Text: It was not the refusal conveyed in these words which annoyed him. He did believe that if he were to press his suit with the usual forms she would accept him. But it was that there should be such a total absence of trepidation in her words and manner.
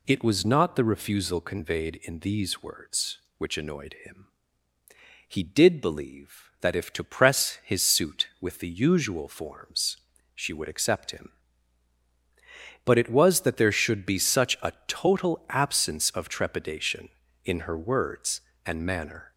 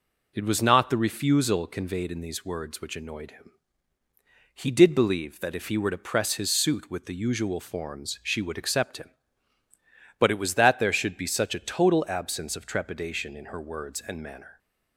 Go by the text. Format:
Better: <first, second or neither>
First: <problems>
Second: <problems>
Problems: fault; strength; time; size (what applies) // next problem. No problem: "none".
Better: second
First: skips "he were"; at 6.9 s // pauses between "forms" and "she"; at 9.9 s; 0.40 s long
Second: none